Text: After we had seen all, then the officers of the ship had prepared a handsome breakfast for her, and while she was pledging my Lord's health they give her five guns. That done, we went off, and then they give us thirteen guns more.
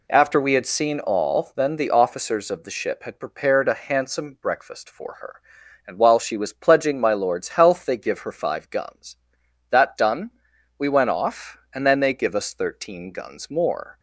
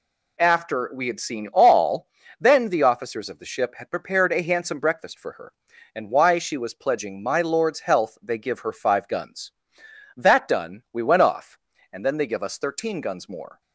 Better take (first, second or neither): first